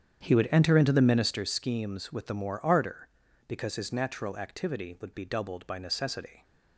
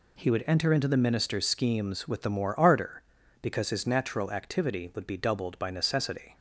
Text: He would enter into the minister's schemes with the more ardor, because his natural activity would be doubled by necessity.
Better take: second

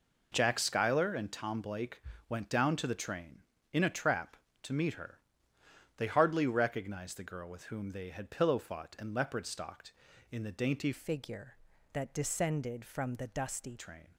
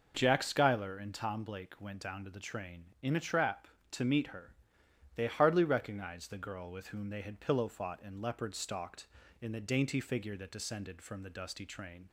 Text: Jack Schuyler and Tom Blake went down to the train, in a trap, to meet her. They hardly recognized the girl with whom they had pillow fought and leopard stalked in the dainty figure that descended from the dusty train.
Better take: second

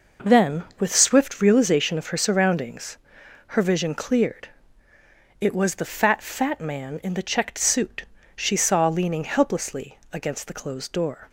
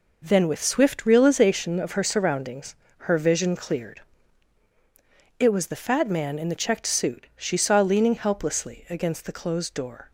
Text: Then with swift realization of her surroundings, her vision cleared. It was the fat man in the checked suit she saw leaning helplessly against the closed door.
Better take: second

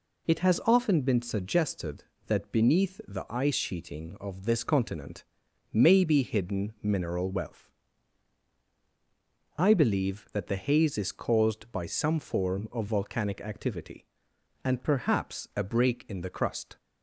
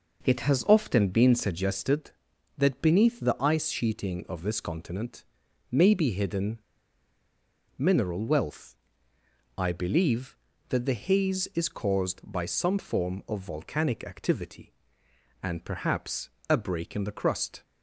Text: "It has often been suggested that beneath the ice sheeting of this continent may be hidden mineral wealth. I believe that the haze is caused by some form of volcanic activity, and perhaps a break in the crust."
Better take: first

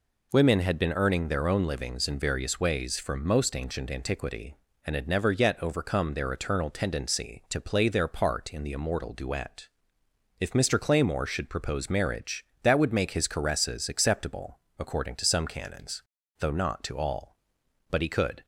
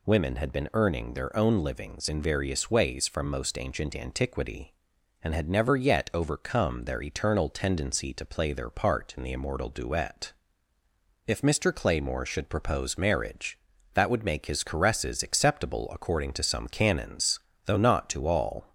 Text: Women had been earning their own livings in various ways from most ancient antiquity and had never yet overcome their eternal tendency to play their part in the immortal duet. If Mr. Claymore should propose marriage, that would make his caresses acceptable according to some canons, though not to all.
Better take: second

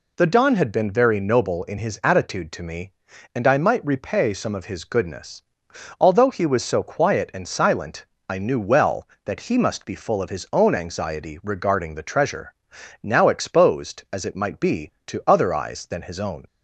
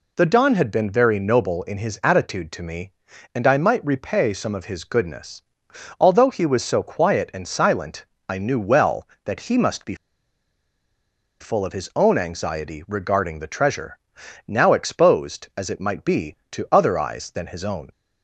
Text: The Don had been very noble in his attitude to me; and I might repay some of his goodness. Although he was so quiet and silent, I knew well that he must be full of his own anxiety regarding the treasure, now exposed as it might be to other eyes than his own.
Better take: first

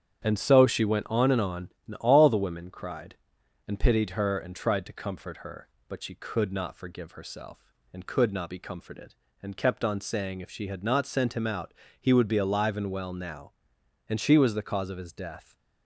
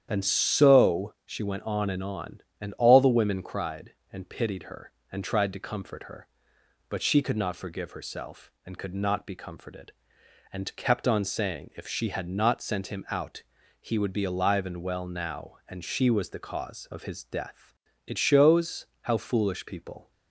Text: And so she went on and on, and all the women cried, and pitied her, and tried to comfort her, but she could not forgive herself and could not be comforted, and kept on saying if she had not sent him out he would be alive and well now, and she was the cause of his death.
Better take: first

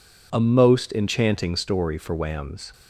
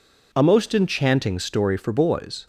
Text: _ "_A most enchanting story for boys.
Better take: second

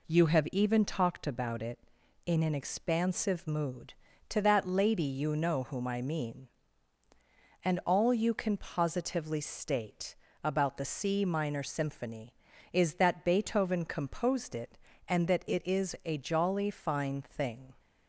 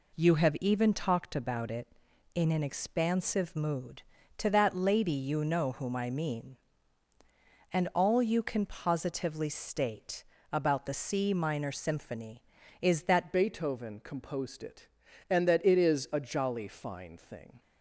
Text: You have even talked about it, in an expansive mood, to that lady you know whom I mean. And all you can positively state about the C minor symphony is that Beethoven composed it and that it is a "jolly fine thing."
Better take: first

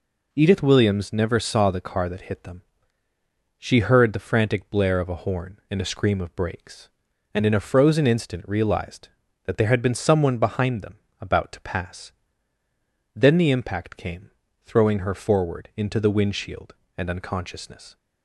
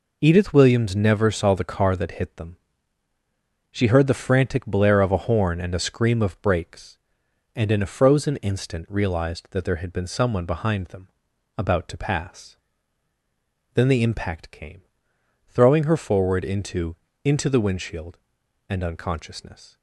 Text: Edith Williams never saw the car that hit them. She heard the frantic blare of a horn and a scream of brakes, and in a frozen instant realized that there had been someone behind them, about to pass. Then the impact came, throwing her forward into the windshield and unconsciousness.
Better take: first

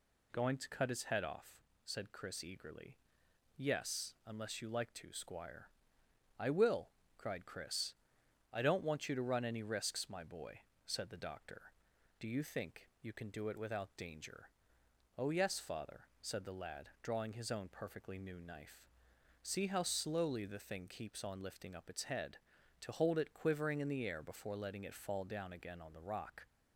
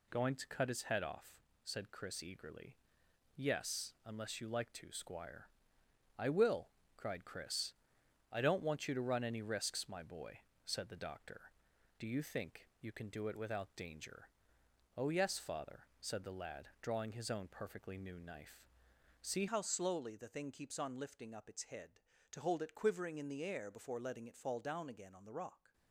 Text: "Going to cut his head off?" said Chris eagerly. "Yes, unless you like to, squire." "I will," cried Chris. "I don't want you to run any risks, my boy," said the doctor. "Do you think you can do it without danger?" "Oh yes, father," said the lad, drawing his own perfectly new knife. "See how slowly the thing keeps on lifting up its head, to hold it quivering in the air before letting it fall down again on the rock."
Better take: first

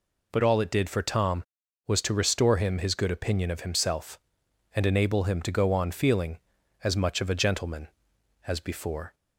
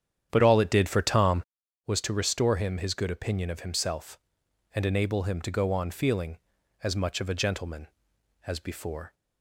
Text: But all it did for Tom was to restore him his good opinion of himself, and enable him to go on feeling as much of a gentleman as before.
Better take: first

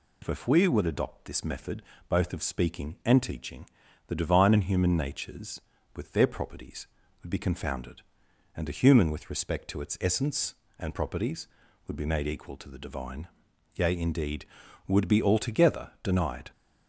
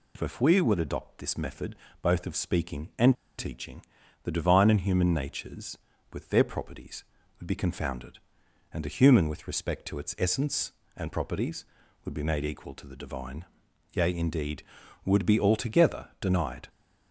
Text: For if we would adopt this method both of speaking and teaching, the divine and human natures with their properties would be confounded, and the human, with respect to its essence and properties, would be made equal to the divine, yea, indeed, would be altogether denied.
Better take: first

